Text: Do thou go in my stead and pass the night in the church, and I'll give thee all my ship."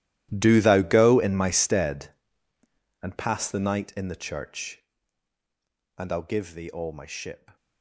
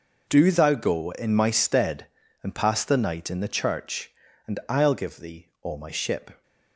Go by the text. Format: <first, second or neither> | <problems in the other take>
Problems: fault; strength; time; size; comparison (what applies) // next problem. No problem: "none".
second | gets quieter; strong; throughout; 18.5 dB